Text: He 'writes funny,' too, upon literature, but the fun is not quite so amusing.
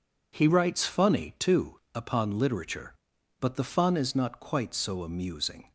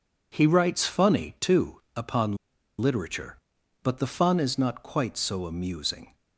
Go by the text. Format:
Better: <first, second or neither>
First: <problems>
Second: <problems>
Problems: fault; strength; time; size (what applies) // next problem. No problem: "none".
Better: first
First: none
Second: pauses between "upon" and "literature"; at 2.3 s; 0.43 s long